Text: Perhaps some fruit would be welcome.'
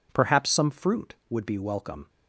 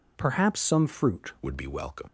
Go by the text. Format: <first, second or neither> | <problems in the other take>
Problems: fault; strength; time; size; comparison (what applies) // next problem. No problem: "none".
first | changes voice at "would"; from 1.4 s on; 0.6 s long